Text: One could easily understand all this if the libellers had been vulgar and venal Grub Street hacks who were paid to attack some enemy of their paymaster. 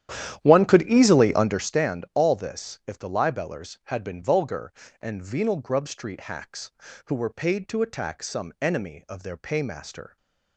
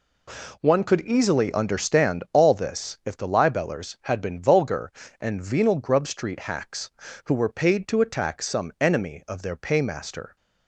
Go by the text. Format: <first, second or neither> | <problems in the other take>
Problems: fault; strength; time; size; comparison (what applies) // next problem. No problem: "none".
second | starts louder than the rest; strong; until 1.7 s; 11 dB // stays silent after the last word; slight; from 10.0 s on; 0.5 s long